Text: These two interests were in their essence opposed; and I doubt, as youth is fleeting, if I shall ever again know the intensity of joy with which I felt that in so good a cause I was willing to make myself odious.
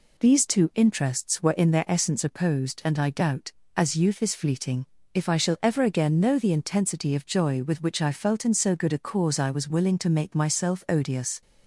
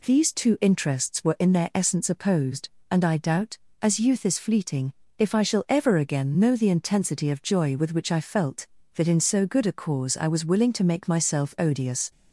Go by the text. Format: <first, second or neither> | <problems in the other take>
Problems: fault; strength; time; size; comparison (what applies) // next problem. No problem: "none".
second | skips "that"; at 8.4 s